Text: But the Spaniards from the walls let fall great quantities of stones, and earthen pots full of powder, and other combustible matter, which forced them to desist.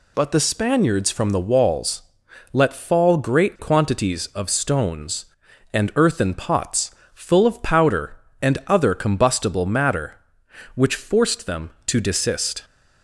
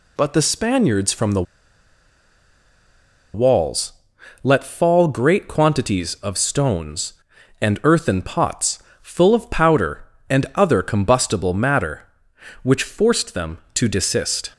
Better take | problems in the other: first | pauses between "the" and "walls"; strong; at 1.4 s; 1.9 s long // pauses between "walls" and "let"; noticeable; at 3.9 s; 0.52 s long; noticeable in the first // pauses between "pots" and "full"; slight; at 8.7 s; 0.22 s long; slight in the first

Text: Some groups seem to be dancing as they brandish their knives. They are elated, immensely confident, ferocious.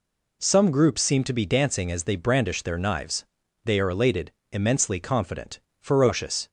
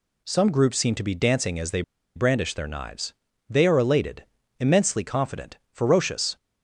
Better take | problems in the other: first | pauses between "they" and "brandish"; slight; at 1.8 s; 0.34 s long

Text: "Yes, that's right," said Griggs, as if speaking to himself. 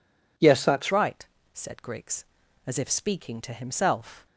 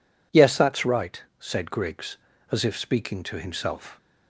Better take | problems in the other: second | changes voice at "right"; from 0.9 s on; 3.3 s long

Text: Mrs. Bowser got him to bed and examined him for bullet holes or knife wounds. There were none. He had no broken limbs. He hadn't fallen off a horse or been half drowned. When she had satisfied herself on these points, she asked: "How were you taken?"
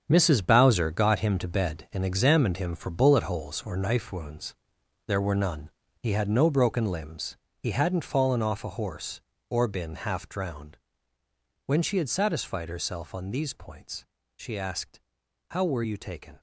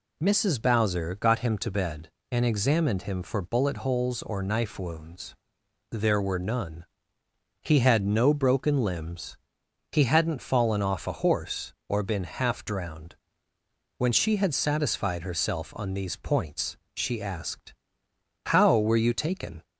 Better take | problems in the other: second | gets quieter; strong; throughout; 10 dB

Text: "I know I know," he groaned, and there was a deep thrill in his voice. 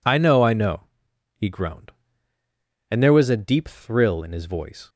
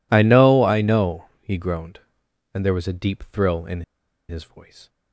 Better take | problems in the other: first | pauses between "in" and "his"; noticeable; at 3.8 s; 0.47 s long

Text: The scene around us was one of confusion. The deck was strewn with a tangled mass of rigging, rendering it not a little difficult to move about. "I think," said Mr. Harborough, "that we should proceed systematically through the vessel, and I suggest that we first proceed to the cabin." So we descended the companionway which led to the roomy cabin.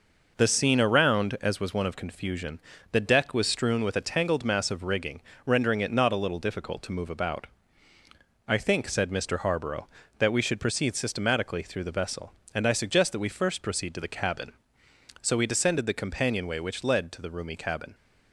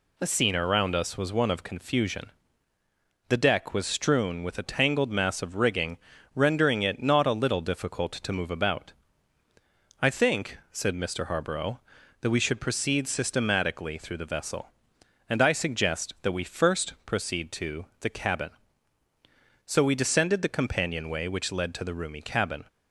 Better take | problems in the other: second | says "as" for "us"; at 1.4 s

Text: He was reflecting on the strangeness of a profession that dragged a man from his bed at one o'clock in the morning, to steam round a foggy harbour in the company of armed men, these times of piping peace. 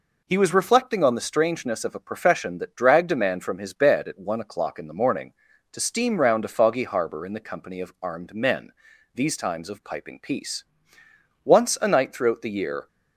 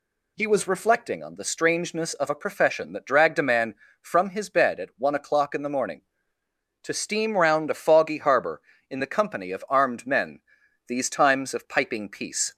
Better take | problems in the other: second | goes on to say "Once a night throughout the year"; from 11.4 s on; 1.4 s long

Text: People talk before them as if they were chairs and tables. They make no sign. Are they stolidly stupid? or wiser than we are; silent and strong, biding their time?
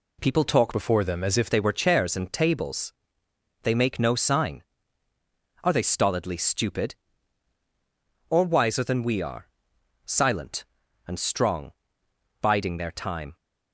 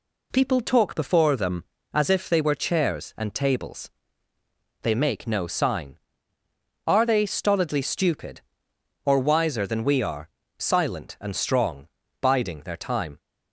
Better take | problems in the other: second | changes voice from "before" to "if"; from 0.7 to 1.4 s; 0.7 s long

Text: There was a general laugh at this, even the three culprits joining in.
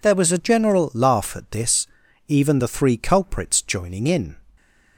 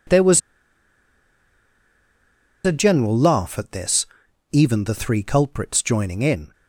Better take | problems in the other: first | pauses between "was" and "a"; strong; at 0.3 s; 2.2 s long

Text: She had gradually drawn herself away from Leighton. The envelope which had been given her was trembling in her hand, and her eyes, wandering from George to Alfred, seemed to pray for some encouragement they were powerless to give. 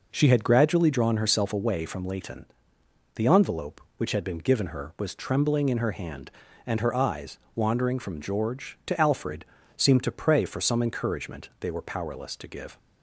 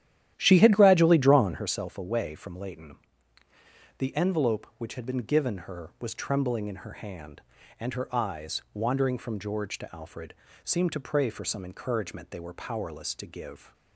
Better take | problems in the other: first | starts louder than the rest; strong; until 1.8 s; 12 dB

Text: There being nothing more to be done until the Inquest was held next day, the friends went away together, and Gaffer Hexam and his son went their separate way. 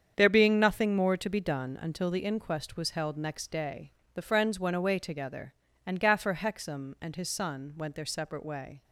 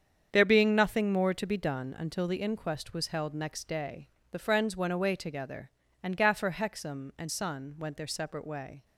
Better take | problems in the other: first | starts louder than the rest; strong; until 1.3 s; 7.5 dB; strong in the first // skips "his"; at 7.3 s

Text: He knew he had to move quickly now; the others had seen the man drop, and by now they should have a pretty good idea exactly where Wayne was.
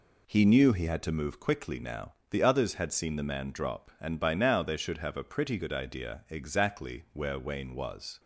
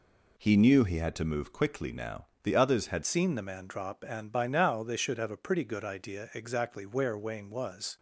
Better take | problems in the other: first | changes voice at "seen"; from 3.0 s on; 4.9 s long

